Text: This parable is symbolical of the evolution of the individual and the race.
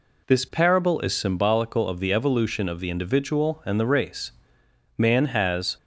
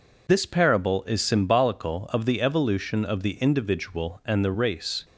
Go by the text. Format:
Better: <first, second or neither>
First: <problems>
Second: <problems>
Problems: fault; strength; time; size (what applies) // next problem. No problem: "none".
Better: second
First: goes on to say "Man has"; noticeable; from 4.9 s on; 0.78 s long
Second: none